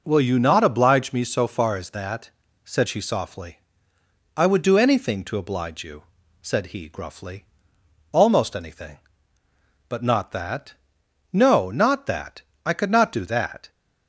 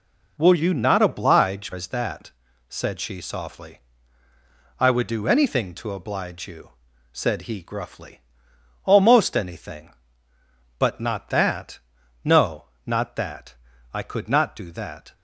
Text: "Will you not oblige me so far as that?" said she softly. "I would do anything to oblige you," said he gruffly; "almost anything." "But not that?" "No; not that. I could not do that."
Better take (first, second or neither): first